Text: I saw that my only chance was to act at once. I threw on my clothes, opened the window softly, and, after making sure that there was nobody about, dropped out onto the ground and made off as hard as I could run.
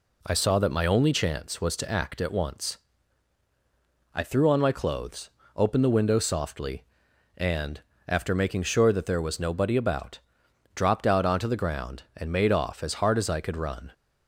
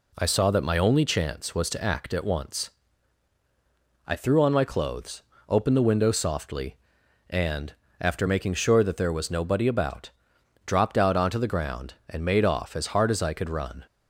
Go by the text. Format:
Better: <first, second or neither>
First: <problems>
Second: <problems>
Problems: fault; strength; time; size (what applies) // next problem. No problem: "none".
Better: neither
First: none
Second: none